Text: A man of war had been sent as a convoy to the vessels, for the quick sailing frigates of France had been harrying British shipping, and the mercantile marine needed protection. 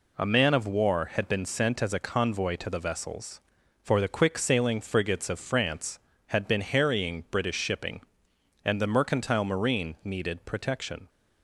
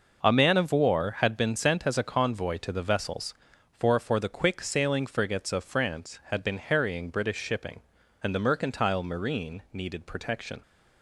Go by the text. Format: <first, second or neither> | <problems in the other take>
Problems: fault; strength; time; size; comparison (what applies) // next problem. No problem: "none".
first | says "for" twice; at 3.9 s